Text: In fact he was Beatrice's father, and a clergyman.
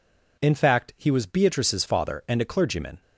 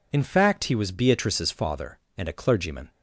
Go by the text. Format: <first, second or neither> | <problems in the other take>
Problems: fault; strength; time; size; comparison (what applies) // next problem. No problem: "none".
neither | none